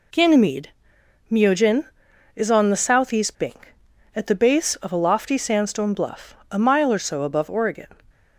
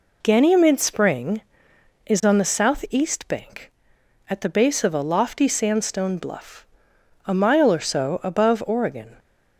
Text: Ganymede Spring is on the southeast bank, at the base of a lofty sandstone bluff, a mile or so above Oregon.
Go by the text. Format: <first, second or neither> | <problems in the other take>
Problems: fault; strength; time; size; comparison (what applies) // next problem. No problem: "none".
second | says "Myojin" for "Spring"; at 1.2 s